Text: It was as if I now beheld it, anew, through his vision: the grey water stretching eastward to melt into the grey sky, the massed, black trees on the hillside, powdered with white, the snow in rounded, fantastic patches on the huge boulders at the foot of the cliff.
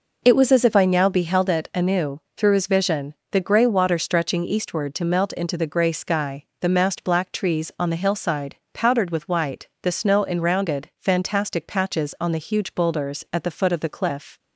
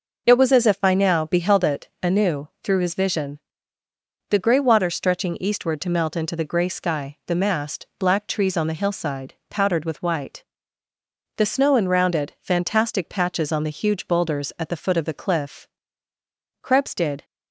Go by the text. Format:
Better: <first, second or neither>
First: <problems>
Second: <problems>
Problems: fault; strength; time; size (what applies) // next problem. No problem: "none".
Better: first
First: none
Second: goes on to say "Krebs did"; noticeable; from 16.6 s on; 0.62 s long